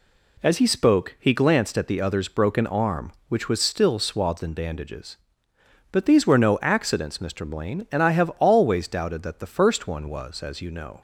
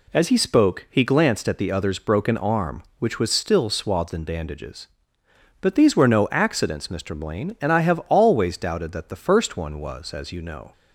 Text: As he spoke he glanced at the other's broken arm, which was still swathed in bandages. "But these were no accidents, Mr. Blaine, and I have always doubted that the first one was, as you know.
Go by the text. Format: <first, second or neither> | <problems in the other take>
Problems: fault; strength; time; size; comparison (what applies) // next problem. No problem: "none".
neither | none